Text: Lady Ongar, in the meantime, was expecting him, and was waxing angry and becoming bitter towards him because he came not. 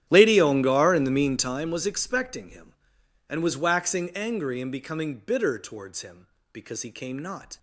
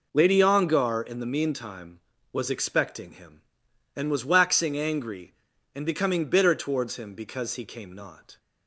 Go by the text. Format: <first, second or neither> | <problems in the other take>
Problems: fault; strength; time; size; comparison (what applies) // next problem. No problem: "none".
second | starts louder than the rest; strong; until 1.7 s; 11 dB